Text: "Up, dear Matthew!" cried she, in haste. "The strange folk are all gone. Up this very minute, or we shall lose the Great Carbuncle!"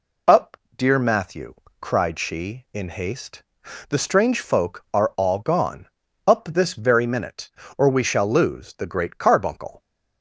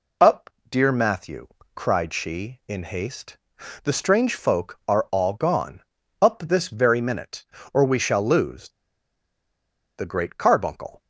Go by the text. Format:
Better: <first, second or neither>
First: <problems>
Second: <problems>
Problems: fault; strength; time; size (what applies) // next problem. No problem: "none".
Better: first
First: none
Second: pauses between "lose" and "the"; strong; at 8.6 s; 1.2 s long